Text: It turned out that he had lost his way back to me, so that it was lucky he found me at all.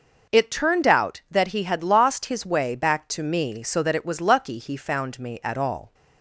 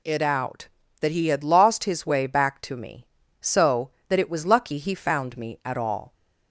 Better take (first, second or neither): first